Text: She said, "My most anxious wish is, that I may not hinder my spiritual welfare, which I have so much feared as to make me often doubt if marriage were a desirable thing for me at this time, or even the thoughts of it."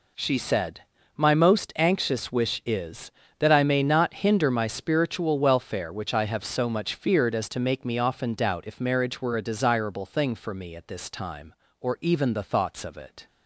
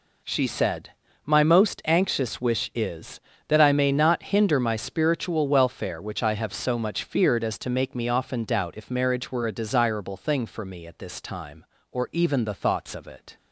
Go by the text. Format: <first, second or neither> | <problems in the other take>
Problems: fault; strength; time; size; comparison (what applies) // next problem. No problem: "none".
neither | none